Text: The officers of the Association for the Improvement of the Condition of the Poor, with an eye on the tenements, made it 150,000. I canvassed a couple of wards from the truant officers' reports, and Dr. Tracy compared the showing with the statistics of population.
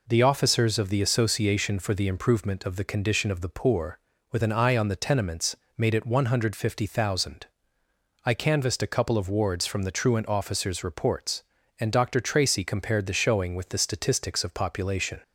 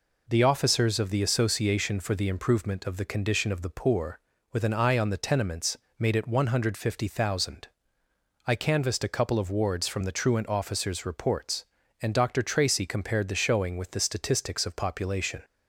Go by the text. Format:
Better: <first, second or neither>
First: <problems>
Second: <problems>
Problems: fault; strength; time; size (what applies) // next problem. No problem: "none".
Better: neither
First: none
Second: none